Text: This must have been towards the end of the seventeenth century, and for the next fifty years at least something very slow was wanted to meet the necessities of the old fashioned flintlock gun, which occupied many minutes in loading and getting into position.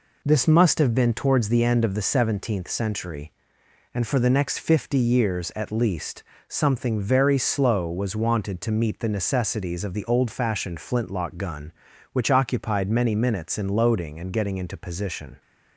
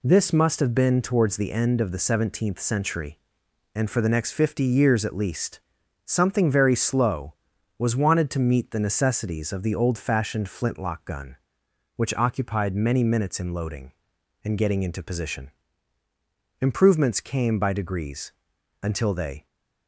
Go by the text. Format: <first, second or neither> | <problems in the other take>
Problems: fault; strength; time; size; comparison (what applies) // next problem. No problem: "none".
first | pauses between "least" and "something"; noticeable; at 5.5 s; 0.50 s long; slight in the first // goes on to say "Improvements came by degrees until they"; strong; from 16.6 s on; 2.8 s long